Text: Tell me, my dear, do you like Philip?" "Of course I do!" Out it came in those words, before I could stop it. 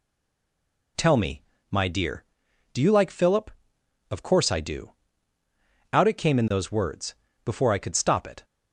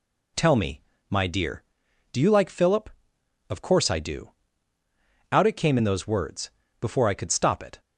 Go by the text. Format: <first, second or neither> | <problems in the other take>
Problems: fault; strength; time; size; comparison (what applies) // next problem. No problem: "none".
second | stays silent before the first word; slight; until 0.9 s; 0.9 s long